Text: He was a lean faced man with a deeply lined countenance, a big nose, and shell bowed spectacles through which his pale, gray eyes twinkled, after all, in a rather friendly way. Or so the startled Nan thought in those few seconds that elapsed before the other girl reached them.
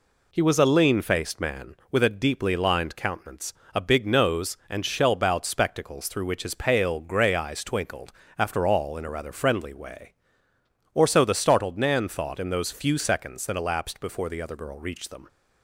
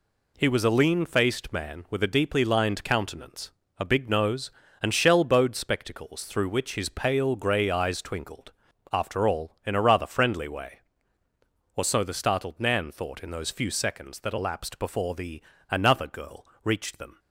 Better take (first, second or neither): first